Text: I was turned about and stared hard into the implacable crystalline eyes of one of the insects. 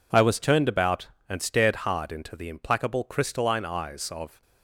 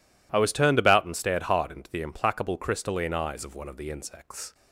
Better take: second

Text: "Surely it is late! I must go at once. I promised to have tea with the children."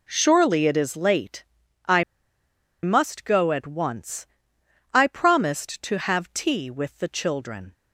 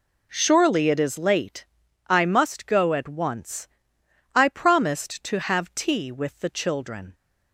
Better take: second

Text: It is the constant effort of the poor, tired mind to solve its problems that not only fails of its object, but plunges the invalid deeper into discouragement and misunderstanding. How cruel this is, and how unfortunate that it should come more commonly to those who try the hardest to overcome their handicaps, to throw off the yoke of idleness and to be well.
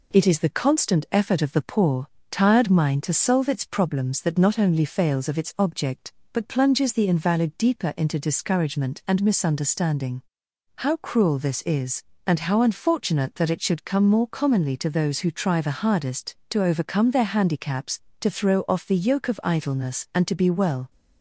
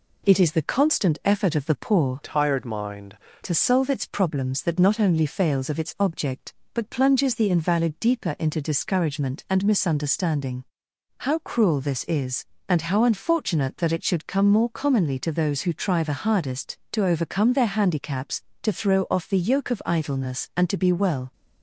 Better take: first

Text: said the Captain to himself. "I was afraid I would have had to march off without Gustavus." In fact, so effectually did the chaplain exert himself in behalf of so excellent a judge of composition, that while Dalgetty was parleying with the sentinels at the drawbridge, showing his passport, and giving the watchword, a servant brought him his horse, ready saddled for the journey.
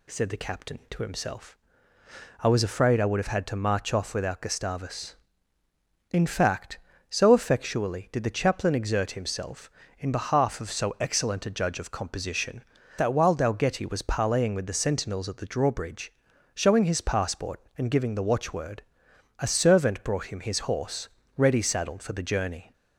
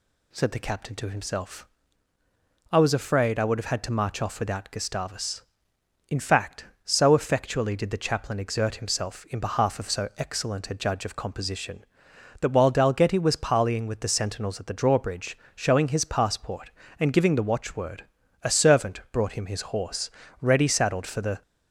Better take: first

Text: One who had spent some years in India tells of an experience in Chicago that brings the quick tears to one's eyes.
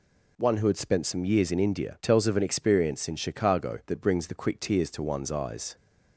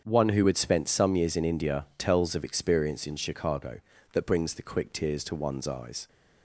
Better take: first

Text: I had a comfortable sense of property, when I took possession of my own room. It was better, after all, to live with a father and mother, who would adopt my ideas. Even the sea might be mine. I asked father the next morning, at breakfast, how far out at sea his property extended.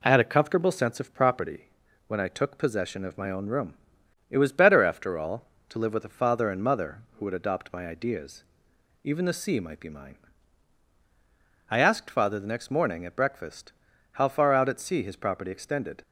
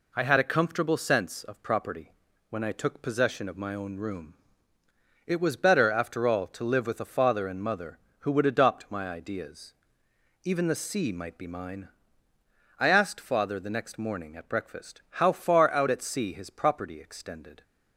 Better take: neither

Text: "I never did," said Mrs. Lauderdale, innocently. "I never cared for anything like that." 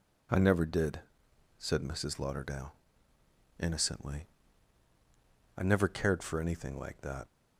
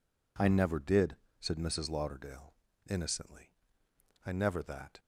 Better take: first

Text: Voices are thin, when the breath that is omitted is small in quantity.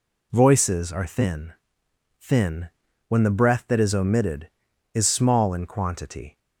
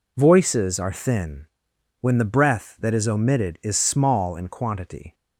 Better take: second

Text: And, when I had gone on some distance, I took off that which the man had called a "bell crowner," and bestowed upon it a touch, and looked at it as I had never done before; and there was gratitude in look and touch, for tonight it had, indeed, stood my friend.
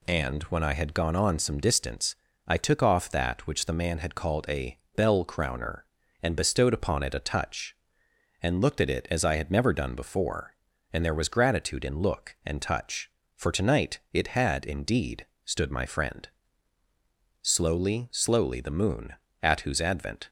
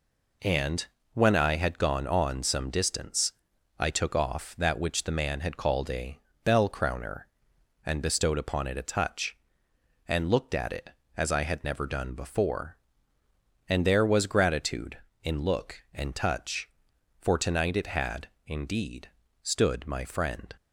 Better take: second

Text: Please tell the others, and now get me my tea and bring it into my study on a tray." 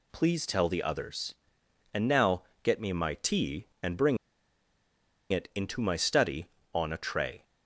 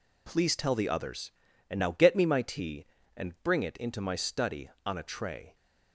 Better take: second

